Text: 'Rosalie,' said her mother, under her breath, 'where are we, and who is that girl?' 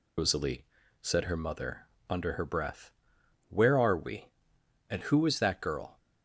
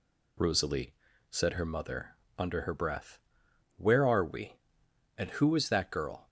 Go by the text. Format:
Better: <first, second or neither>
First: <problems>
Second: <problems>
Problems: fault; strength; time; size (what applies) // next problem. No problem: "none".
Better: second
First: loses the start of "Rosalie"; at 0.1 s; 90 ms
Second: none